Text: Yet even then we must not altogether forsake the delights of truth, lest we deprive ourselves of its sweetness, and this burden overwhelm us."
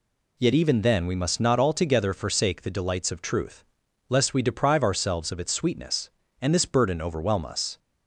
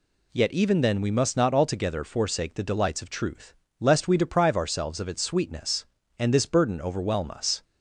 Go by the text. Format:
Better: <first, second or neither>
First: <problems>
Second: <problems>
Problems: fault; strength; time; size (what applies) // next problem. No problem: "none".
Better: neither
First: none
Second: none